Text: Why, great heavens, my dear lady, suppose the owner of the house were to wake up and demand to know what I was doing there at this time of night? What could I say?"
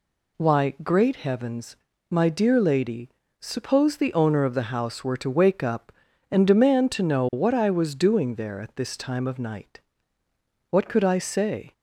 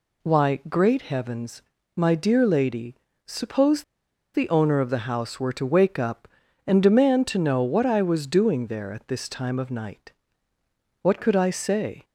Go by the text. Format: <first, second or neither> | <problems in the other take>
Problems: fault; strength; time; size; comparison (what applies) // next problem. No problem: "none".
first | pauses between "suppose" and "the"; noticeable; at 3.8 s; 0.50 s long